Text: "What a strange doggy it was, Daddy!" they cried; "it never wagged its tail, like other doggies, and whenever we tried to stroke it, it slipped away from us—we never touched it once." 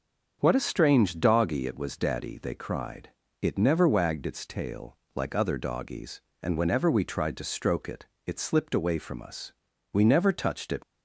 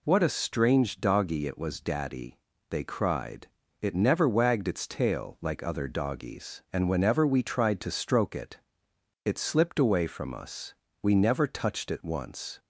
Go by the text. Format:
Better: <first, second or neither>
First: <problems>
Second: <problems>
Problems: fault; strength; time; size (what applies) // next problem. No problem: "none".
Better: second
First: starts louder than the rest; until 1.4 s; 6.5 dB // stops before "once"; at 10.8 s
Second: none